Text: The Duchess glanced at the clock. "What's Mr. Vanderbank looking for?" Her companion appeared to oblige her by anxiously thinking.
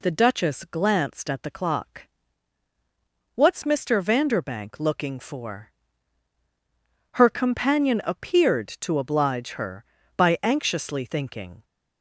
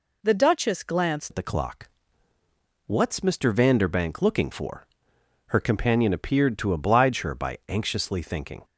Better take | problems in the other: first | changes voice at "at"; from 1.2 s on; 7.4 s long

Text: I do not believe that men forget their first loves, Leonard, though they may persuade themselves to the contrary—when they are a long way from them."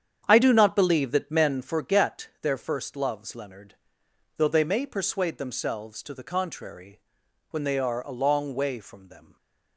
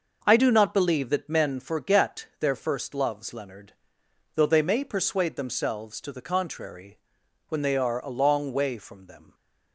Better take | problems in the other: second | starts louder than the rest; strong; until 2.0 s; 8.5 dB

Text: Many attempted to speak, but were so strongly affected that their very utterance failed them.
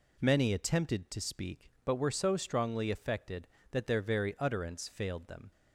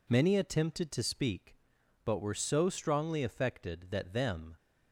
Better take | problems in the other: first | skips "their very utterance failed"; at 4.1 s

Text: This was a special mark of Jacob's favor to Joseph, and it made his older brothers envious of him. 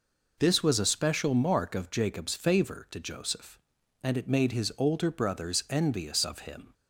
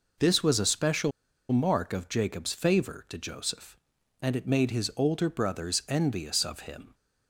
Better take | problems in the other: first | pauses between "special" and "mark"; at 1.1 s; 0.40 s long

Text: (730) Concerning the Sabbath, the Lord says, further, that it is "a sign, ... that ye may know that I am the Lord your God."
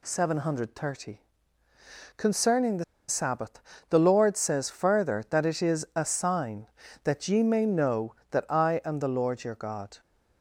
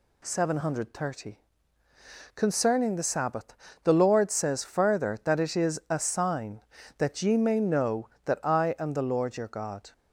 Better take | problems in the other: second | pauses between "the" and "Sabbath"; slight; at 2.8 s; 0.24 s long

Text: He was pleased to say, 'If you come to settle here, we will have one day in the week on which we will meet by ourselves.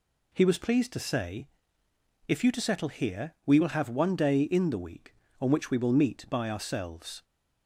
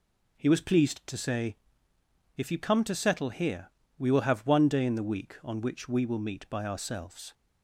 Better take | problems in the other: second | skips "come"; at 2.5 s

